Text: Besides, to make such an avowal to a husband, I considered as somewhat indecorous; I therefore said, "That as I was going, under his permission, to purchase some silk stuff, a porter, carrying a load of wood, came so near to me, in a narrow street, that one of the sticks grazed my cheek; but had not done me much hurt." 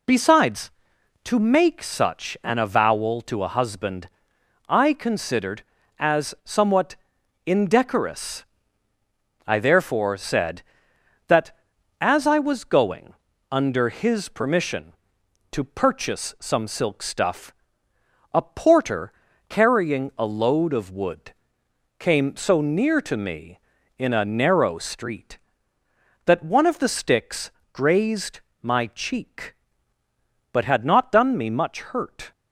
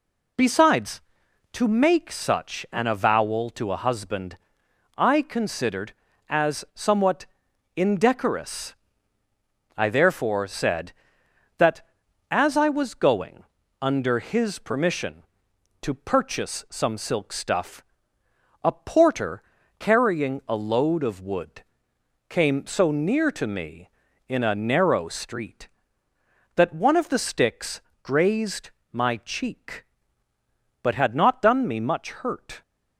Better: neither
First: pauses between "somewhat" and "indecorous"; noticeable; at 6.9 s; 0.50 s long // pauses between "sticks" and "grazed"; slight; at 27.5 s; 0.22 s long // pauses between "grazed" and "my"; slight; at 28.3 s; 0.22 s long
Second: pauses between "somewhat" and "indecorous"; noticeable; at 7.2 s; 0.50 s long // pauses between "sticks" and "grazed"; slight; at 27.8 s; 0.22 s long // pauses between "grazed" and "my"; slight; at 28.6 s; 0.22 s long

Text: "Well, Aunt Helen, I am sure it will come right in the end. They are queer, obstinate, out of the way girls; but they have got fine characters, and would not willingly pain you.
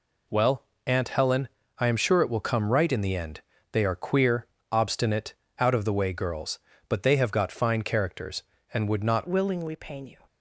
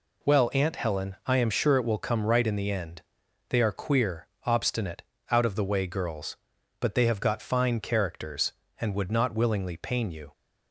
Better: second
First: changes voice at "willingly"; from 9.2 s on; 0.9 s long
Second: none

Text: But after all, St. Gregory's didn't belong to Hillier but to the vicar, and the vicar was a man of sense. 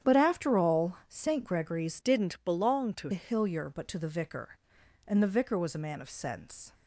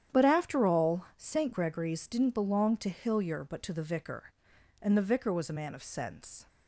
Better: second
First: starts louder than the rest; strong; until 1.1 s; 9.5 dB // changes voice from "didn't" to "to"; from 2.0 to 3.0 s; 1.0 s long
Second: starts louder than the rest; strong; until 1.2 s; 9.5 dB

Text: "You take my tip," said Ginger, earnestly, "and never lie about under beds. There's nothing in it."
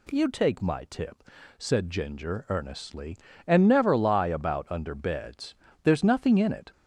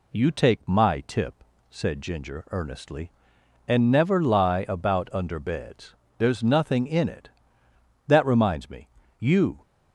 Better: first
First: none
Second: goes on to say "That reminds me You"; from 8.0 s on; 1.5 s long

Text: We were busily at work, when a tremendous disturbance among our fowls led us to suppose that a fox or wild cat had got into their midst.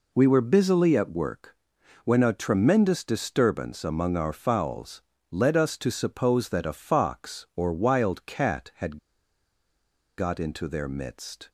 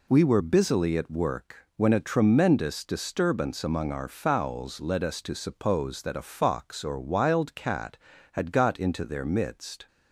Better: second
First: pauses between "fowls" and "led"; slight; at 5.0 s; 0.28 s long // pauses between "had" and "got"; at 8.9 s; 1.2 s long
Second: none

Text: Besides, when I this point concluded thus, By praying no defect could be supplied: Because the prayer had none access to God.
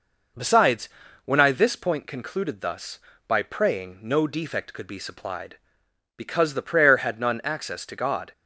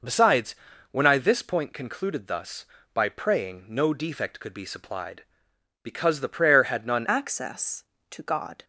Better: first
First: none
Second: changes voice at "access"; from 7.0 s on; 1.6 s long

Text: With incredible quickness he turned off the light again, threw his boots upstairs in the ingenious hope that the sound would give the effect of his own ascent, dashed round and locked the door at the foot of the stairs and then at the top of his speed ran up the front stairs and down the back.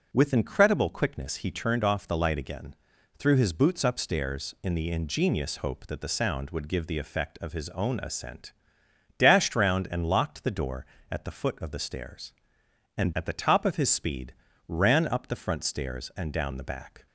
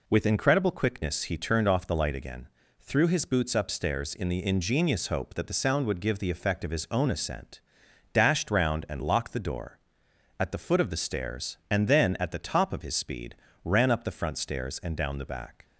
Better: second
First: skips "then"; at 13.1 s // pauses between "speed" and "ran"; slight; at 14.3 s; 0.34 s long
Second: pauses between "speed" and "ran"; slight; at 13.3 s; 0.30 s long

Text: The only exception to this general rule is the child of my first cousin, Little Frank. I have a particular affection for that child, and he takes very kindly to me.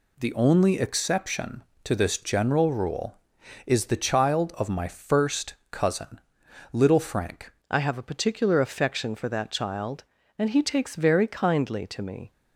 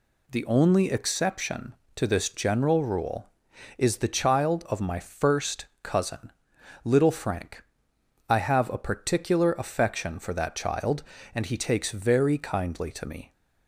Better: second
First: pauses between "first" and "cousin"; slight; at 5.5 s; 0.18 s long // changes voice at "I"; from 7.7 s on; 4.6 s long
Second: pauses between "first" and "cousin"; slight; at 5.6 s; 0.18 s long

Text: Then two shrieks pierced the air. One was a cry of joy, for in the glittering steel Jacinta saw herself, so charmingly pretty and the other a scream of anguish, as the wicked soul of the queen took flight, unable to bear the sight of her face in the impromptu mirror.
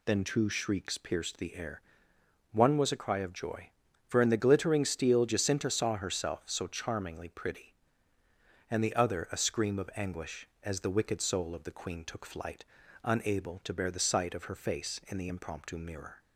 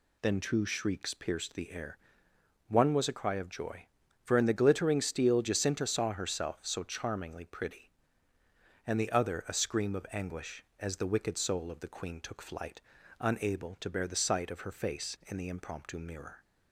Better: neither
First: none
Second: none

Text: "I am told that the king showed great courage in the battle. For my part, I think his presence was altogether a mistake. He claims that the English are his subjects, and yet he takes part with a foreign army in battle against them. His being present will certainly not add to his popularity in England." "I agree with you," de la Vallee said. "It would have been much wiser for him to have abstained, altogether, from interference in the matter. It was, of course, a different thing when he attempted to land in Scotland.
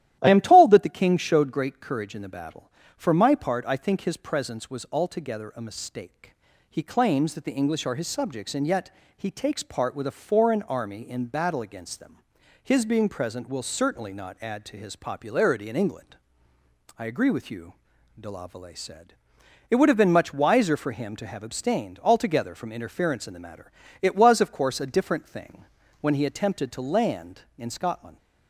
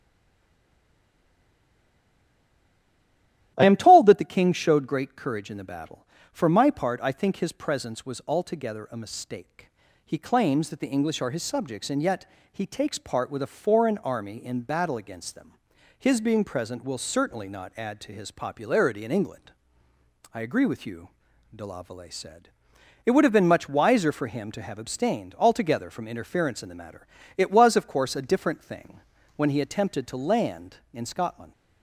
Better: first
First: starts louder than the rest; strong; until 1.2 s; 13 dB // pauses between "yet" and "he"; slight; at 8.9 s; 0.26 s long // pauses between "thing" and "when"; slight; at 25.6 s; 0.36 s long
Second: stays silent before the first word; strong; until 3.5 s; 3.5 s long // starts louder than the rest; strong; until 4.5 s; 13 dB // pauses between "yet" and "he"; slight; at 12.2 s; 0.26 s long // pauses between "thing" and "when"; slight; at 28.9 s; 0.36 s long

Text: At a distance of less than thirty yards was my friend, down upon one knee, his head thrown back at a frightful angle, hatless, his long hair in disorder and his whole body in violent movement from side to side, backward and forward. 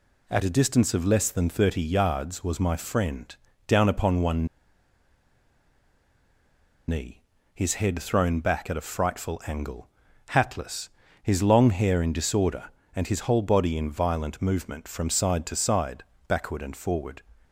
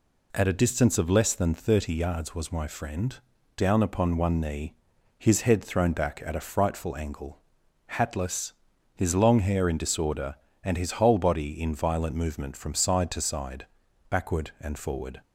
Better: second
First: pauses between "one" and "knee"; strong; at 4.4 s; 2.4 s long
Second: none

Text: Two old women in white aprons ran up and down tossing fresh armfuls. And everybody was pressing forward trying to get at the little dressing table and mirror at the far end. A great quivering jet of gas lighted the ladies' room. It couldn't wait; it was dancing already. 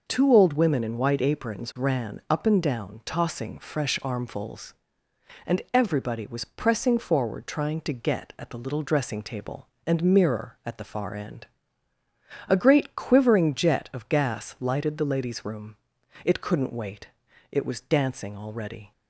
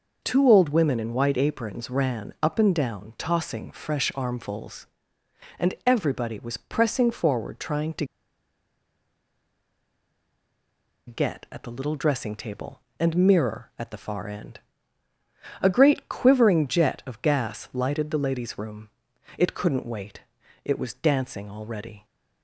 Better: first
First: none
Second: pauses between "to" and "get"; strong; at 8.0 s; 3.0 s long

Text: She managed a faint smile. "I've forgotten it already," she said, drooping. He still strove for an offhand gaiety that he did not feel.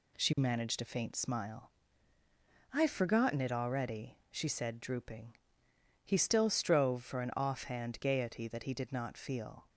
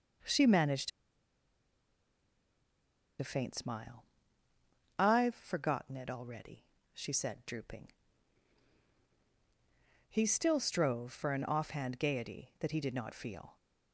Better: first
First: none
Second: pauses between "managed" and "a"; strong; at 0.9 s; 2.3 s long

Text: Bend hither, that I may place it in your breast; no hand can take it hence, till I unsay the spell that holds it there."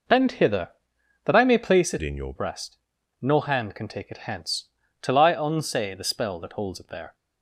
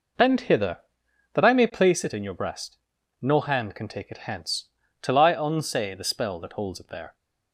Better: second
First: changes voice from "in" to "your"; from 2.0 to 2.3 s; 0.3 s long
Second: none

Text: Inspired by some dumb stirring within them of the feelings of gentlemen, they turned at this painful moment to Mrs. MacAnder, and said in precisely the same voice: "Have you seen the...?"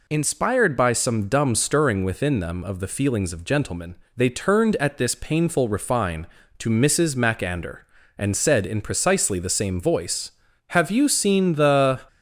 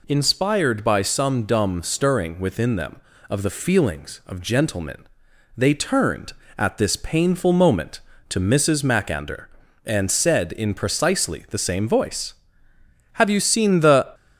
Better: second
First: says "refine" for "moment"; at 5.6 s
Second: none

